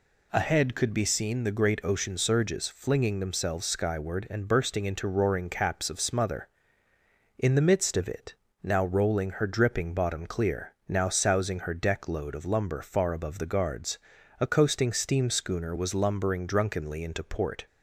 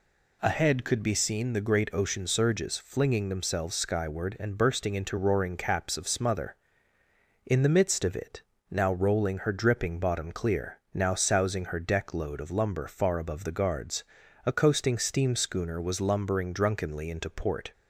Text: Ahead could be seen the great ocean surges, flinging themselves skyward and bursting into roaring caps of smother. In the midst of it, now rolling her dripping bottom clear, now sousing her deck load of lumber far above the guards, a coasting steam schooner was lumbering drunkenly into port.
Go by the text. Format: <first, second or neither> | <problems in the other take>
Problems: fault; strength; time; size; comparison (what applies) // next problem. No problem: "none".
neither | none